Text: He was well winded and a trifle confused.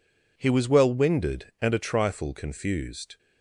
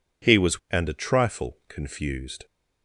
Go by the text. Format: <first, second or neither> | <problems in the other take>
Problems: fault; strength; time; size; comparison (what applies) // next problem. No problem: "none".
first | skips "well winded"; at 0.6 s